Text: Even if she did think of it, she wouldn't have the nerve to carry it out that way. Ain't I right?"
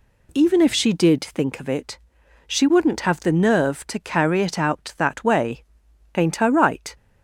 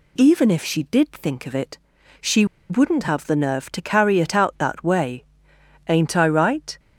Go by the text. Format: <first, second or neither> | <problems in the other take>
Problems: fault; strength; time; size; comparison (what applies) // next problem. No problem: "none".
first | pauses between "she" and "wouldn't"; slight; at 2.4 s; 0.25 s long